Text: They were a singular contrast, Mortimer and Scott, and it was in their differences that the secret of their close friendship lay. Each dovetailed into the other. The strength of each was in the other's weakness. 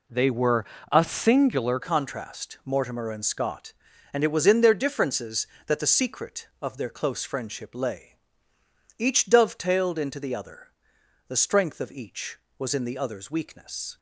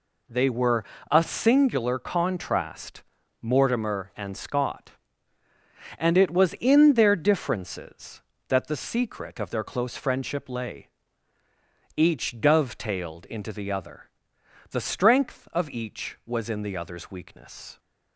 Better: second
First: pauses between "were" and "a"; slight; at 0.6 s; 0.28 s long // changes voice at "contrast"; from 1.8 s on; 12.1 s long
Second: pauses between "were" and "a"; slight; at 0.8 s; 0.28 s long

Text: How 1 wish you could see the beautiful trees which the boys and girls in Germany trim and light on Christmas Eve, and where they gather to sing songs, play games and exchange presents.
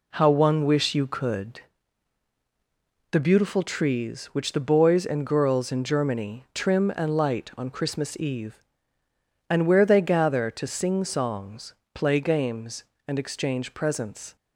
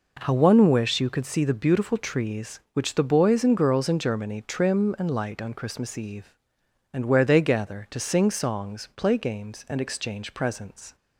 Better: second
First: skips "see"; at 2.3 s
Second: none

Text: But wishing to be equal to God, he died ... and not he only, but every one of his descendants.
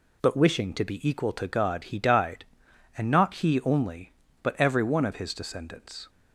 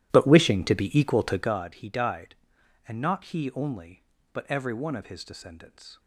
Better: first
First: none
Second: starts louder than the rest; strong; until 1.6 s; 13.5 dB

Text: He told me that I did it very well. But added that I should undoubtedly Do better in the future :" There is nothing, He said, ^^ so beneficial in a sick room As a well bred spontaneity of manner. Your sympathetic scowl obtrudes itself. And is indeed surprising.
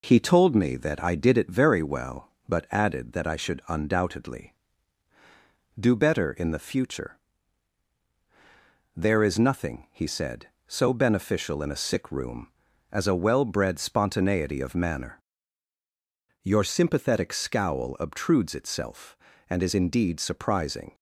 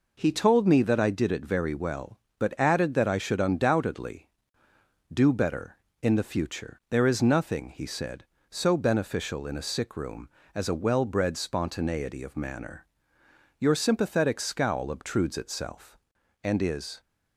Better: first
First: none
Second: stops before "indeed surprising"; at 17.0 s

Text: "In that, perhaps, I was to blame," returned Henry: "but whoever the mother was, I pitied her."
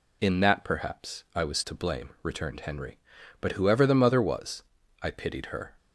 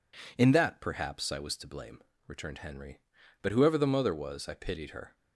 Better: neither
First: none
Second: none

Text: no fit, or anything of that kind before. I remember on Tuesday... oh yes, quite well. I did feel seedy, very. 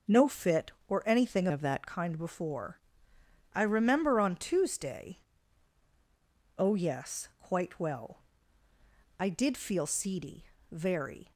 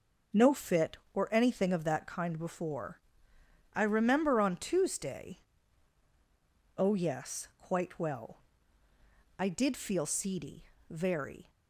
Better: second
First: changes voice from "of" to "that"; from 1.5 to 1.8 s; 0.3 s long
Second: none

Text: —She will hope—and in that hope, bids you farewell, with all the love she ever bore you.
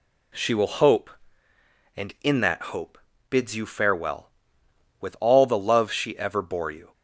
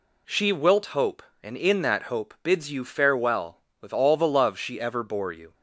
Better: first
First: none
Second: says "wilt" for "will"; at 0.5 s

